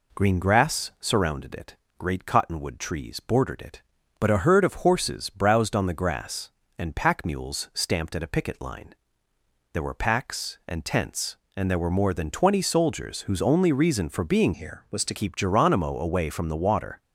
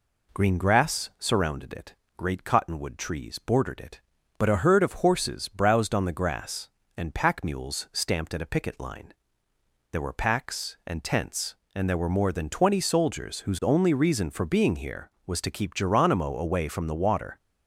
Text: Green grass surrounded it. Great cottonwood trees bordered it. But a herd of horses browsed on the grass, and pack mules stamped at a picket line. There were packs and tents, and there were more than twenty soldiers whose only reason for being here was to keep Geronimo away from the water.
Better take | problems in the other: second | changes voice from "here" to "to"; from 14.5 to 15.1 s; 0.6 s long

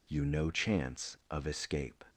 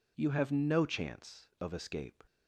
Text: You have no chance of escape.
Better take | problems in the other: second | skips "have"; at 0.2 s

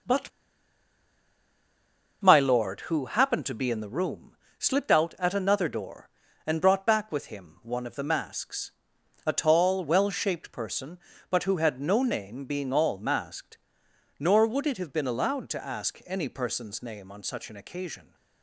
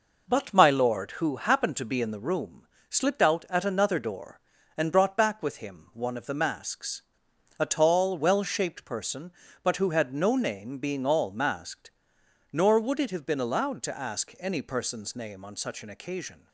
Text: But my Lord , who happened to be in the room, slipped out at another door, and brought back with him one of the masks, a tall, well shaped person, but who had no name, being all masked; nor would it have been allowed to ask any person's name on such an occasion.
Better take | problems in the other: second | pauses between "But" and "my"; strong; at 0.2 s; 1.9 s long

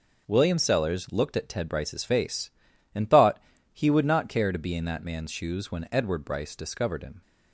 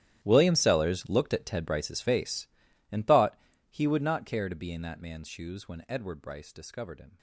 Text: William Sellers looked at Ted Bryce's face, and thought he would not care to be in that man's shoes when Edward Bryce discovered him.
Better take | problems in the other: first | gets quieter; strong; throughout; 19.5 dB // pauses between "thought" and "he"; slight; at 3.3 s; 0.32 s long; slight in the first

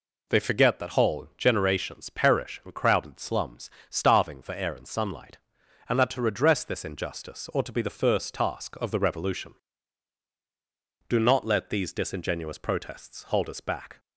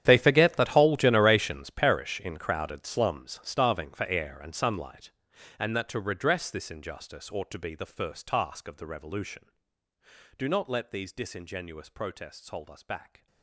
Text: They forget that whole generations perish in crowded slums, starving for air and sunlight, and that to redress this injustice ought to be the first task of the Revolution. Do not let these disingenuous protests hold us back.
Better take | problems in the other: first | gets quieter; strong; throughout; 18.5 dB

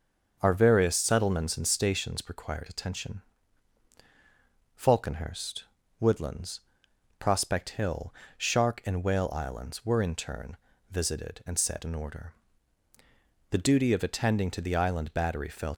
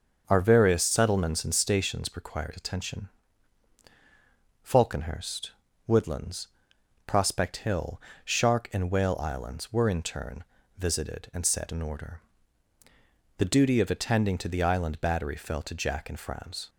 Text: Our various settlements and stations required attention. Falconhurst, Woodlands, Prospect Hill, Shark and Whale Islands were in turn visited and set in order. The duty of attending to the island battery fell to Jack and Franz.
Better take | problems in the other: second | starts louder than the rest; until 1.4 s; 6.5 dB; also in the second // pauses between "turn" and "visited"; slight; at 10.5 s; 0.36 s long; slight in the second // stops before "to Jack and Franz"; at 15.7 s

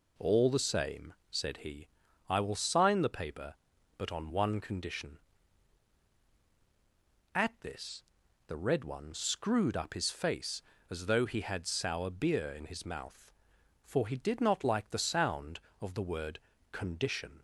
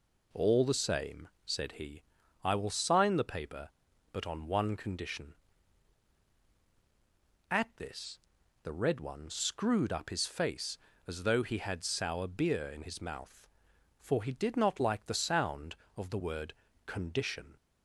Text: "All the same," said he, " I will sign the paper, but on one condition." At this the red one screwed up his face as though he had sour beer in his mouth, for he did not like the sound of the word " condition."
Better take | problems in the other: neither | pauses between "this" and "the"; the same in both

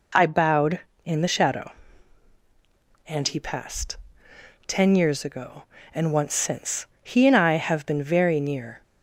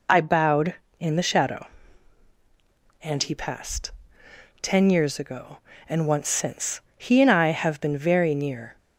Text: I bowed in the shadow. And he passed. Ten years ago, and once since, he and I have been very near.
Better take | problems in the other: first | loses the start of "I"; at 0.0 s; 20 ms

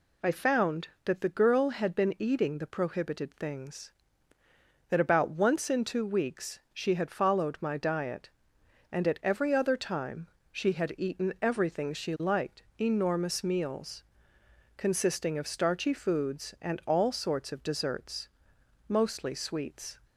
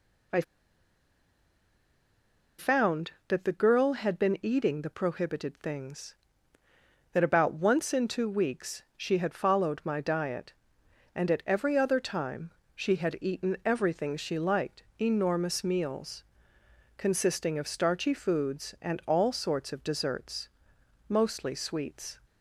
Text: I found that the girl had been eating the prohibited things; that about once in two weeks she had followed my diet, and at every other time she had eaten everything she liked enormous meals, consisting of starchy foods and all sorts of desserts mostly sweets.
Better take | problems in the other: first | pauses between "I" and "found"; strong; at 0.4 s; 2.1 s long // pauses between "time" and "she"; slight; at 12.4 s; 0.24 s long; slight in the first // pauses between "liked" and "enormous"; slight; at 14.8 s; 0.18 s long; slight in the first // pauses between "desserts" and "mostly"; noticeable; at 20.4 s; 0.60 s long; noticeable in the first

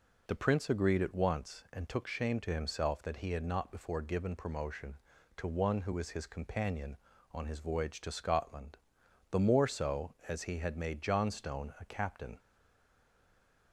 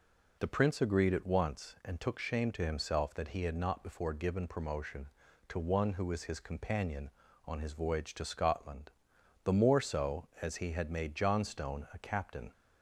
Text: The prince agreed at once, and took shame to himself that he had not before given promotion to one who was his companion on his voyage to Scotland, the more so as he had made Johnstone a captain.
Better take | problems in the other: second | stays silent after the last word; noticeable; from 12.3 s on; 1.4 s long

